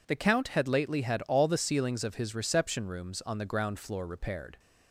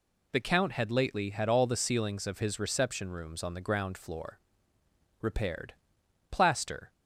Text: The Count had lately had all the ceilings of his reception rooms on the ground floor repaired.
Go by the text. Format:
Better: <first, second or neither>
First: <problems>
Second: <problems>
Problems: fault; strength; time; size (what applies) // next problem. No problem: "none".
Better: first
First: none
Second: pauses between "floor" and "repaired"; noticeable; at 4.3 s; 0.82 s long // goes on to say "Plaster"; noticeable; from 6.2 s on; 0.62 s long